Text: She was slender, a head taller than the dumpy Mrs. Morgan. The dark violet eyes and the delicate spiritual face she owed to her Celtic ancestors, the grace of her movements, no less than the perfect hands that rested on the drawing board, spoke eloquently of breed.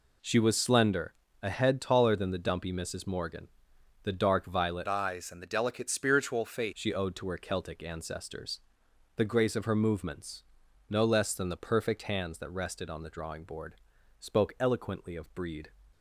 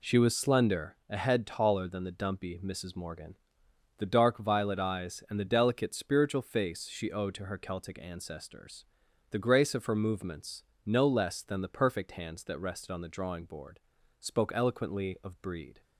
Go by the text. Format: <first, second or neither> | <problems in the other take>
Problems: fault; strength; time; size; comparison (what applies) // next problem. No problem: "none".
second | changes voice from "eyes" to "face"; from 4.8 to 6.7 s; 1.9 s long